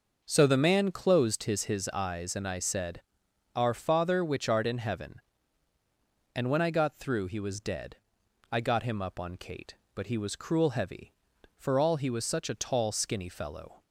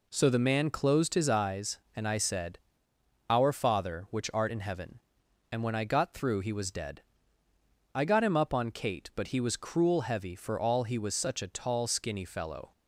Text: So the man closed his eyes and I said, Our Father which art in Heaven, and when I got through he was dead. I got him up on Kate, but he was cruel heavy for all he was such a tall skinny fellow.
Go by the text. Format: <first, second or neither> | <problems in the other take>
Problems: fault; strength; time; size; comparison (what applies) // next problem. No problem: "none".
second | says "his" twice; at 1.6 s